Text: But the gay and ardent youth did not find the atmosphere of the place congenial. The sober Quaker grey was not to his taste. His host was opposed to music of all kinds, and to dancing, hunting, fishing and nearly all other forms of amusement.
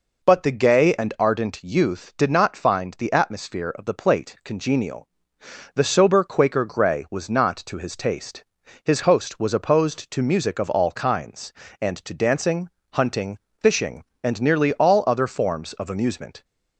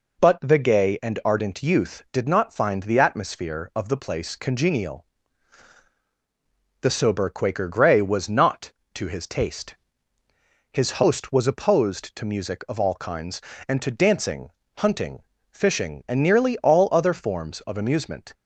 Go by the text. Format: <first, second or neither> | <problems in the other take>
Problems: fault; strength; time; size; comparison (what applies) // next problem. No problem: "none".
second | says "plate" for "place"; at 3.9 s